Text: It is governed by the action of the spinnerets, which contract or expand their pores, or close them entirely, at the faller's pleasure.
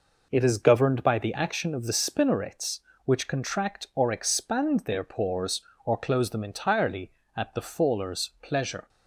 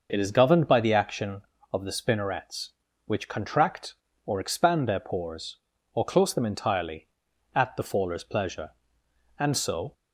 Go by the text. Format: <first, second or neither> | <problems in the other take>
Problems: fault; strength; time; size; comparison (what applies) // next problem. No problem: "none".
first | goes on to say "And so"; from 9.3 s on; 0.54 s long